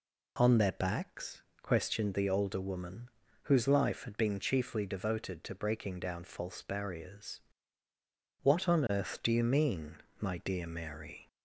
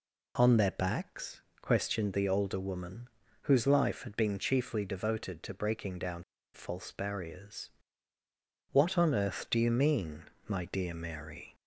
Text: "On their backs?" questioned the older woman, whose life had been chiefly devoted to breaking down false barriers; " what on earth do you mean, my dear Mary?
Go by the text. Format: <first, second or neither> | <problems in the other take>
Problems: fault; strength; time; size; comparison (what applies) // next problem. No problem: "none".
first | pauses between "down" and "false"; slight; at 6.2 s; 0.30 s long